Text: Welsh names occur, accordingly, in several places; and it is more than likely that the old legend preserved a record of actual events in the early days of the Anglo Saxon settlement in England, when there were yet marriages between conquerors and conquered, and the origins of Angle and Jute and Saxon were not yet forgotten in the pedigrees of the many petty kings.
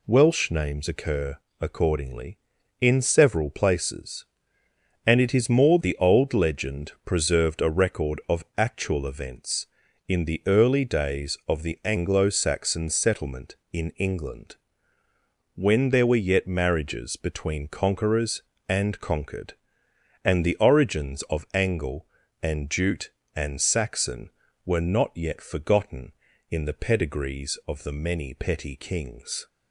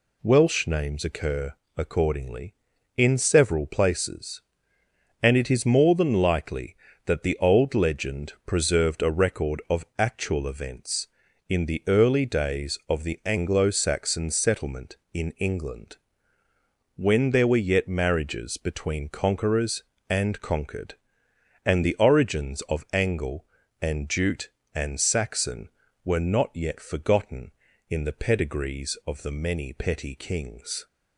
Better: second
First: skips "than likely that"; at 5.8 s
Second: none

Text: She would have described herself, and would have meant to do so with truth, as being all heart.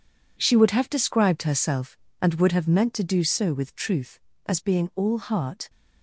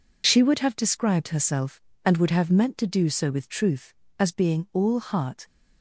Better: second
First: gets quieter; strong; throughout; 11 dB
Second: none

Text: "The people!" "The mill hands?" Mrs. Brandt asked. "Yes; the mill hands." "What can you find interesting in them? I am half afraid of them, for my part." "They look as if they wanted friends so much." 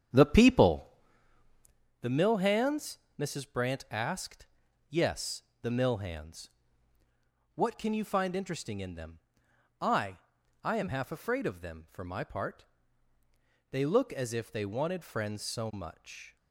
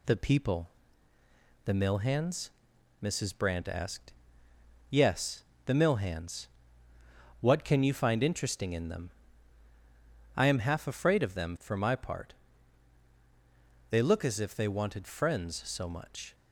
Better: second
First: starts louder than the rest; strong; until 2.2 s; 8.5 dB // says "I" twice; at 10.6 s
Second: none

